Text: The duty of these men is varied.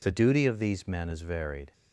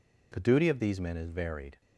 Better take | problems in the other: neither | none

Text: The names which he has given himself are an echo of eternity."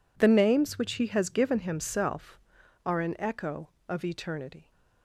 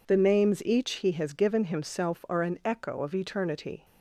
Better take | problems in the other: first | says "each" for "which"; at 0.6 s

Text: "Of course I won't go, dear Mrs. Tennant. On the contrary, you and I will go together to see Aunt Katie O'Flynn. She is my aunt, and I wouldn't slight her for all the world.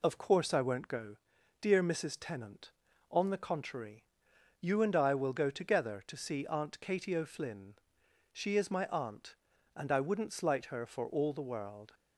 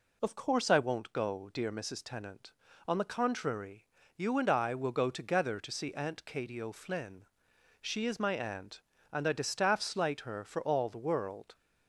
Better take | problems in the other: first | says "distaff" for "wouldn't"; at 9.3 s

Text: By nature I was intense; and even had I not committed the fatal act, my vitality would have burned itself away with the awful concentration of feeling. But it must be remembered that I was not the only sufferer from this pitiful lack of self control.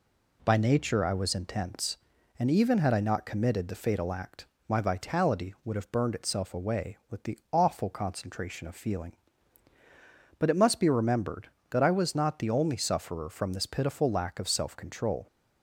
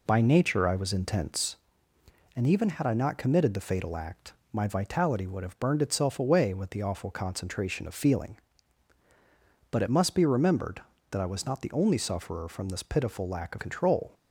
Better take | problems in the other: first | skips "self"; at 13.6 s

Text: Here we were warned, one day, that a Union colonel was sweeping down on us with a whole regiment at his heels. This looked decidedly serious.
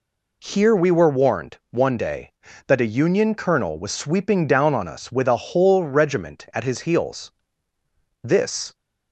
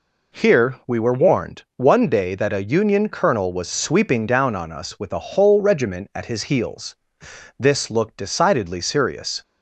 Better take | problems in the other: second | stops before "looked decidedly serious"; at 8.7 s

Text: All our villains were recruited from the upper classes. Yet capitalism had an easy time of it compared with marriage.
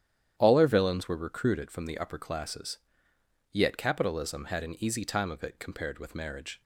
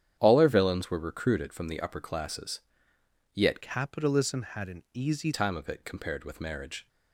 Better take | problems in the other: first | starts louder than the rest; strong; until 1.2 s; 9.5 dB; strong in the first // changes voice from "capitalism" to "easy"; from 3.6 to 5.3 s; 1.7 s long

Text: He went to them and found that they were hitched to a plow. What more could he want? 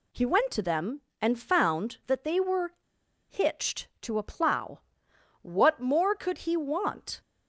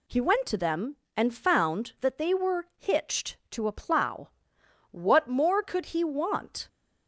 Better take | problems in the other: second | pauses between "were" and "hitched"; noticeable; at 2.7 s; 0.55 s long

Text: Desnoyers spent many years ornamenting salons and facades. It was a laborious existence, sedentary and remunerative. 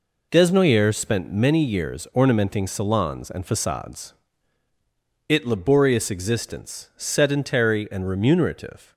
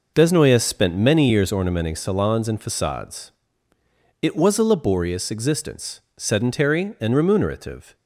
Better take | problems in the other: second | skips "was a"; at 5.4 s

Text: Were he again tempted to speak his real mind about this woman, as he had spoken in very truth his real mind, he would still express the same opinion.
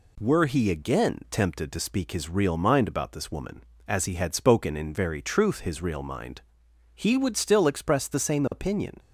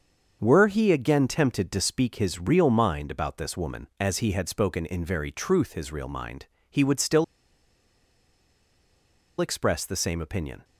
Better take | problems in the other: first | starts louder than the rest; until 1.4 s; 7 dB // pauses between "still" and "express"; strong; at 7.2 s; 2.1 s long

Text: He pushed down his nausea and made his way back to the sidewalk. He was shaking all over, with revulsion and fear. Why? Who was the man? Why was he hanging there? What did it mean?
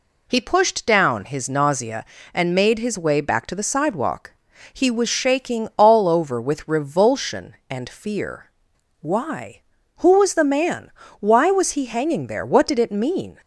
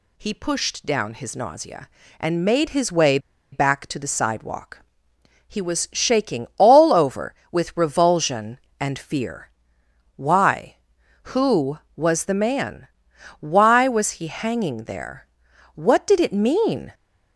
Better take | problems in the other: first | pauses between "way" and "back"; slight; at 3.1 s; 0.33 s long

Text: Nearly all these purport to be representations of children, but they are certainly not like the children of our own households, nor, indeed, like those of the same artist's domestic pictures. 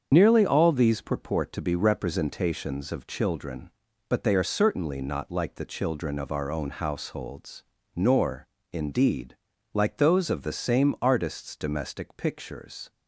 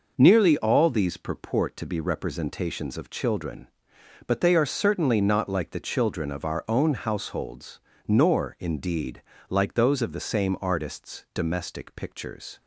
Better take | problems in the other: second | loses the start of "Nearly"; at 0.1 s; 60 ms // starts louder than the rest; strong; until 1.1 s; 7 dB

